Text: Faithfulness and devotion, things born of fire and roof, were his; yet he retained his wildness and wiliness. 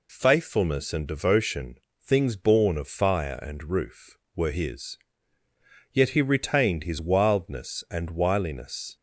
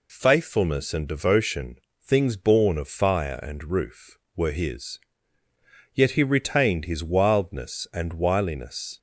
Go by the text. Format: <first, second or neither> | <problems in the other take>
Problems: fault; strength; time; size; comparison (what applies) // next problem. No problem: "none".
neither | none